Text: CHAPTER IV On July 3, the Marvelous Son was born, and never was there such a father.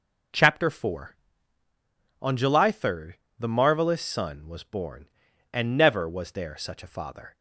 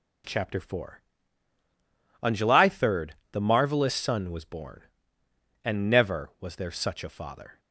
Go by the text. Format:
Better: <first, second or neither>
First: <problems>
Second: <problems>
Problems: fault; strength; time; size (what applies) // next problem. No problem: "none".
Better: neither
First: none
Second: none